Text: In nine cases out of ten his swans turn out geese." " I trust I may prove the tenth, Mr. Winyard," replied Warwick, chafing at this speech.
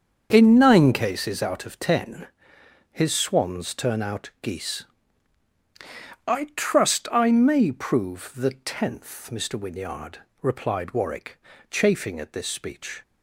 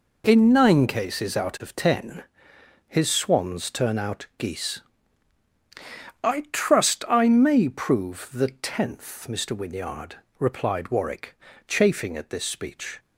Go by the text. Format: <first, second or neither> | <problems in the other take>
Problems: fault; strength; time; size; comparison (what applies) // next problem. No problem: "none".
second | starts louder than the rest; strong; until 1.3 s; 7 dB // pauses between "ten" and "his"; noticeable; at 2.2 s; 0.66 s long; noticeable in the second